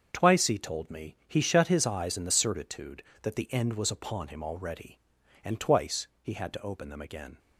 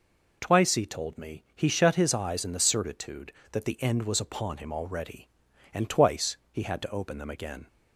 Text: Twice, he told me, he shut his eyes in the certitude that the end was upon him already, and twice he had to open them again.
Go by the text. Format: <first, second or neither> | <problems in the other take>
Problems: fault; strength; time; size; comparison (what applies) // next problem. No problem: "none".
second | gets quieter; strong; throughout; 10 dB // pauses between "twice" and "he"; slight; at 6.0 s; 0.16 s long; slight in the second